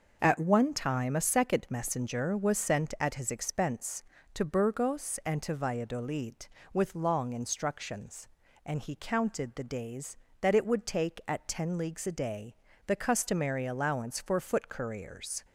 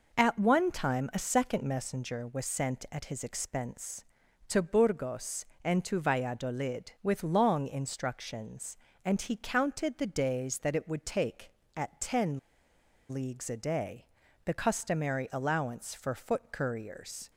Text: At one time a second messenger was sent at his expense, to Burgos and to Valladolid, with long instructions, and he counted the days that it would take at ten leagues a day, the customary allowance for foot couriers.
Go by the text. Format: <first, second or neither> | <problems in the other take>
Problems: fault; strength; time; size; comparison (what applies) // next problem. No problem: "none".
first | pauses between "ten" and "leagues"; noticeable; at 12.3 s; 0.72 s long